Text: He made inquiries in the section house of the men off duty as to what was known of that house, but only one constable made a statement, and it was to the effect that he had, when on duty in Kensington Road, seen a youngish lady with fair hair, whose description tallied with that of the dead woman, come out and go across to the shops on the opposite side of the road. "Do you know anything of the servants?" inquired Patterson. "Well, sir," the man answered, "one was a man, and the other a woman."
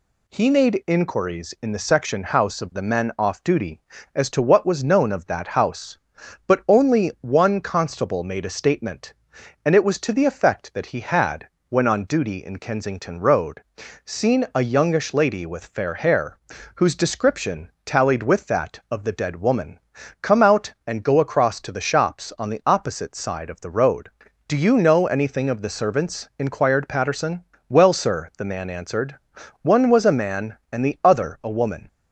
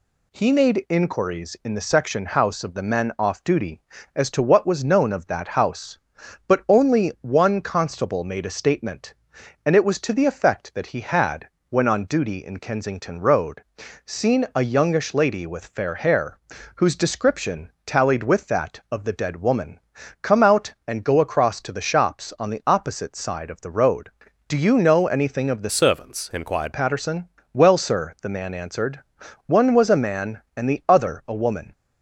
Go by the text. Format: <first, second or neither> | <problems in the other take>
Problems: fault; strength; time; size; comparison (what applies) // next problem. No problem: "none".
first | pauses between "description" and "tallied"; slight; at 17.6 s; 0.16 s long; slight in the first // changes voice from "servants" to "inquired"; from 25.6 to 26.7 s; 1.1 s long